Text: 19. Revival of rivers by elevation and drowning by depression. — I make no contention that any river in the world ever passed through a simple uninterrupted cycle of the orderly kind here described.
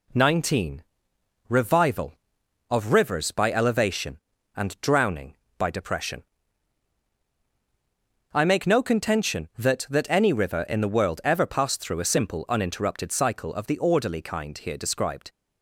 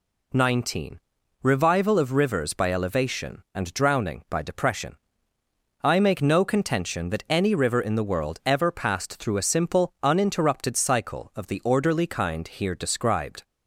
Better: second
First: says "that" twice; at 9.8 s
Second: none

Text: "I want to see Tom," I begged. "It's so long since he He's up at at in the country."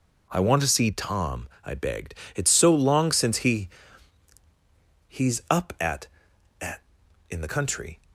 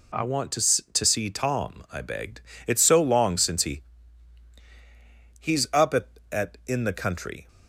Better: first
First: pauses between "he" and "He's"; strong; at 3.6 s; 1.4 s long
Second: says "to" twice; at 0.9 s // pauses between "he" and "He's"; strong; at 3.8 s; 1.5 s long

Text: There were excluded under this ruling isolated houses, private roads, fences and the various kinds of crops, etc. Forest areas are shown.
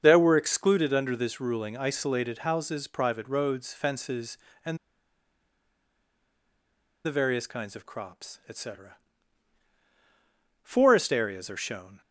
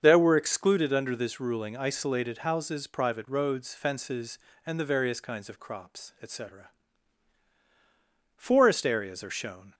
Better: second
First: starts louder than the rest; until 1.0 s; 6.5 dB // pauses between "and" and "the"; strong; at 4.7 s; 2.2 s long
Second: starts louder than the rest; until 1.0 s; 6.5 dB

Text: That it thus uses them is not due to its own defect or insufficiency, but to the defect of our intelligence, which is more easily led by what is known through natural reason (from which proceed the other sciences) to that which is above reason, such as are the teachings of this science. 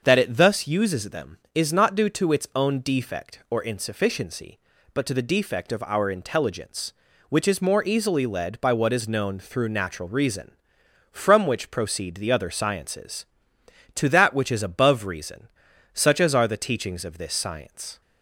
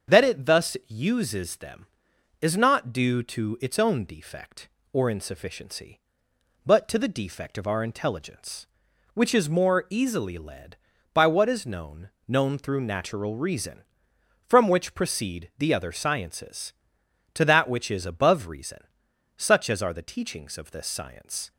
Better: first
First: starts louder than the rest; until 1.0 s; 6.5 dB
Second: starts louder than the rest; until 1.2 s; 7 dB // says "known" twice; at 12.2 s

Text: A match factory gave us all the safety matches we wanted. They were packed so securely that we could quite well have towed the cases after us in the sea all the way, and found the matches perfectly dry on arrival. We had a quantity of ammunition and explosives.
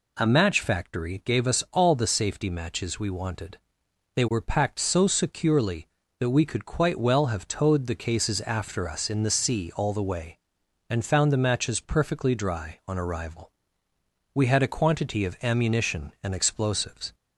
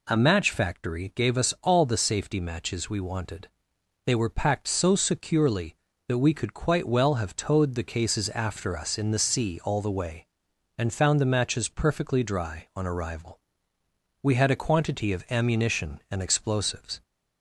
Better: neither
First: none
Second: none

